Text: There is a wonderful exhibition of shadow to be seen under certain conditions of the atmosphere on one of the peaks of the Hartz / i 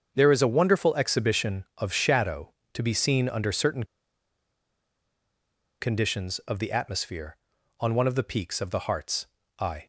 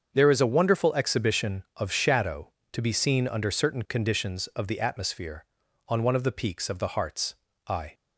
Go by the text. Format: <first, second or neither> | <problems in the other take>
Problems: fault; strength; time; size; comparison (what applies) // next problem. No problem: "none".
second | starts louder than the rest; until 1.1 s; 7 dB; also in the second // pauses between "certain" and "conditions"; strong; at 3.8 s; 1.9 s long